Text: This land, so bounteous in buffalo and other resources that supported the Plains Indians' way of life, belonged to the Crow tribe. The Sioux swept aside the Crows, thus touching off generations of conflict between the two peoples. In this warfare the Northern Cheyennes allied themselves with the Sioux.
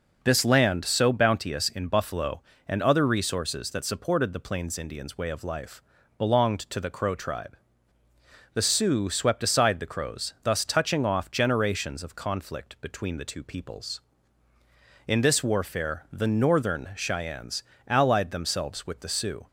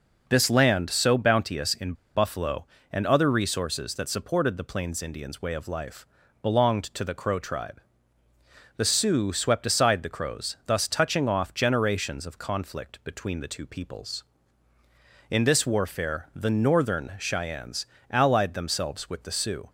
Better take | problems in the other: first | pauses between "in" and "buffalo"; slight; at 1.9 s; 0.21 s long // pauses between "Cheyennes" and "allied"; slight; at 17.8 s; 0.24 s long; slight in the first

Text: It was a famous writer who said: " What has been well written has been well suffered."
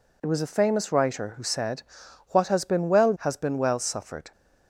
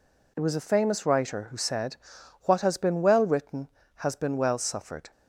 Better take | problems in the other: second | skips "written"; at 3.1 s

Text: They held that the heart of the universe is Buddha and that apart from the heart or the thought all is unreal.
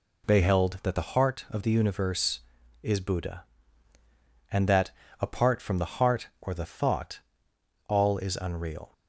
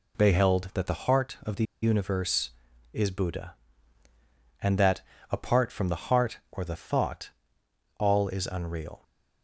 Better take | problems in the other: first | pauses between "the" and "universe"; slight; at 1.6 s; 0.18 s long // pauses between "that" and "apart"; slight; at 5.0 s; 0.28 s long; slight in the first // pauses between "thought" and "all"; noticeable; at 7.3 s; 0.68 s long; noticeable in the first

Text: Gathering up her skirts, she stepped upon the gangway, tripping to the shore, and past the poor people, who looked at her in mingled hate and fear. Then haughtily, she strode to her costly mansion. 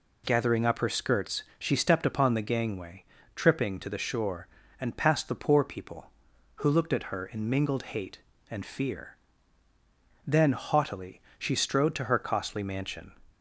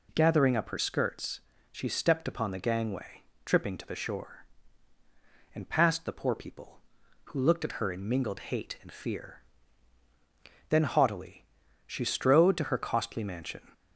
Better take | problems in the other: neither | none

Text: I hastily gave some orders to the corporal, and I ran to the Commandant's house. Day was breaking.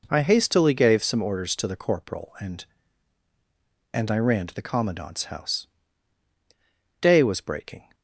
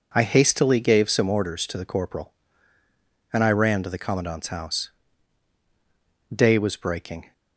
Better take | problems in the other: second | says "and" twice; at 3.9 s

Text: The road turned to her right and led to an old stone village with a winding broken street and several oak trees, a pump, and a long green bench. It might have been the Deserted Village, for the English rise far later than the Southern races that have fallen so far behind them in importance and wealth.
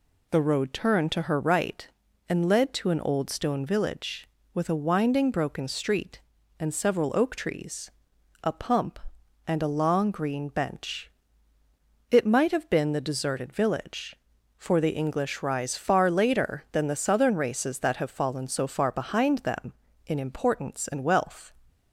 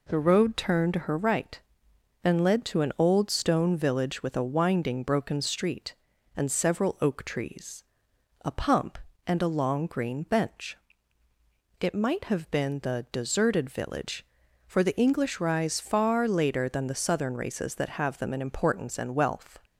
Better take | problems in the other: first | skips "fallen so far behind"; at 18.1 s

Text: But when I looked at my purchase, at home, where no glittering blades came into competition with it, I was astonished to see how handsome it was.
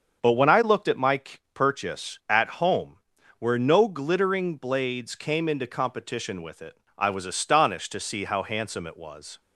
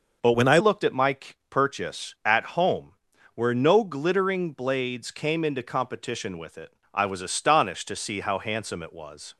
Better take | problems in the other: first | starts louder than the rest; until 1.5 s; 6 dB; also in the first // changes voice from "when" to "I"; from 0.3 to 0.5 s; 0.2 s long // pauses between "my" and "purchase"; slight; at 1.1 s; 0.34 s long; slight in the first

